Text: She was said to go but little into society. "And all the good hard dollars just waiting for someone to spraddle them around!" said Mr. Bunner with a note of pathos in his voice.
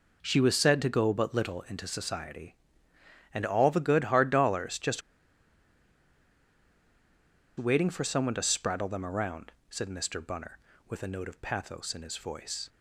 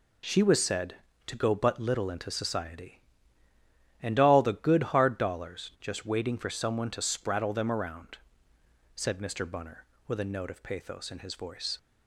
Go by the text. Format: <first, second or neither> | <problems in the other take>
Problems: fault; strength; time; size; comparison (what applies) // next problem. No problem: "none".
second | pauses between "just" and "waiting"; strong; at 5.0 s; 2.5 s long